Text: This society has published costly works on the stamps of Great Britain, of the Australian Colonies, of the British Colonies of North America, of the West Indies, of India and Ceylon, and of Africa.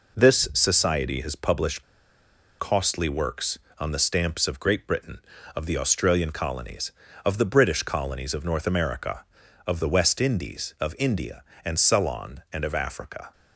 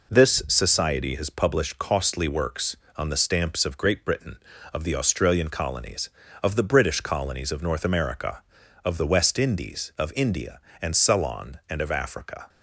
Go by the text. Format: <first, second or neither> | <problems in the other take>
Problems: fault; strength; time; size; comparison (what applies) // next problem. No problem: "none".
second | pauses between "published" and "costly"; noticeable; at 1.8 s; 0.75 s long